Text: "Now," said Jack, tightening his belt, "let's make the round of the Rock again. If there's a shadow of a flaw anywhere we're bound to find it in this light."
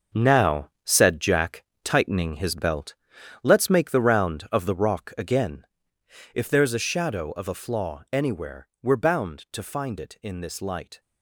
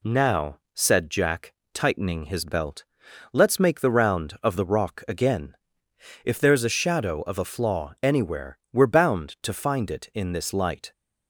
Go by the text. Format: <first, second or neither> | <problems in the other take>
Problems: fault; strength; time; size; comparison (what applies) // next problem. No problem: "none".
second | gets quieter; strong; throughout; 10 dB